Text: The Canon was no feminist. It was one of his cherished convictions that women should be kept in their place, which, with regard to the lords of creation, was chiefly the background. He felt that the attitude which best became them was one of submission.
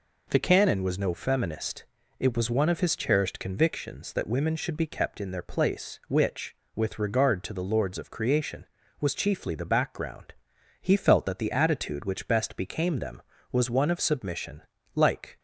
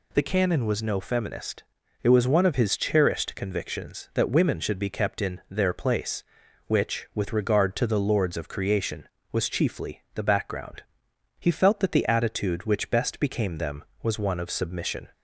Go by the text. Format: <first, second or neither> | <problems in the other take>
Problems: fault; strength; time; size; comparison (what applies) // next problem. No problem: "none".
second | goes on to say "Like"; slight; from 14.9 s on; 0.44 s long